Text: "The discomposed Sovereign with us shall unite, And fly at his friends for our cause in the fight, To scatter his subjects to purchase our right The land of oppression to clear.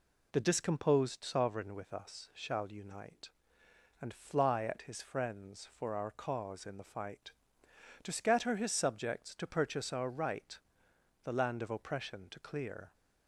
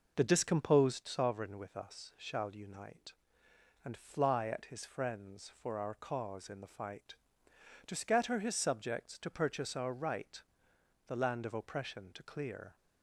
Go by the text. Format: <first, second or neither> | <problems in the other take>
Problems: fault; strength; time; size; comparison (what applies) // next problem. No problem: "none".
first | starts louder than the rest; noticeable; until 1.1 s; 5 dB // pauses between "right" and "The"; noticeable; at 10.4 s; 0.68 s long; noticeable in the first